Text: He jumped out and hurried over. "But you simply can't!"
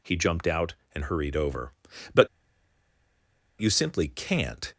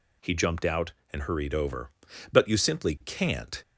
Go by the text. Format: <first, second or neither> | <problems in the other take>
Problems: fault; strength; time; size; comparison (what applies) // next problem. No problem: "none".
second | pauses between "But" and "you"; strong; at 2.2 s; 1.3 s long